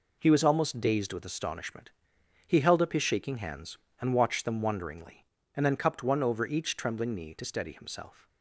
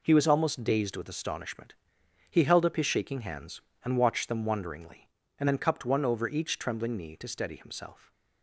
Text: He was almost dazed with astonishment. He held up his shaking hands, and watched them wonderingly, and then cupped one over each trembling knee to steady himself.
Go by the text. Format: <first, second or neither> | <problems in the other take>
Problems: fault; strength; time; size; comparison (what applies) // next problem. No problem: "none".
neither | none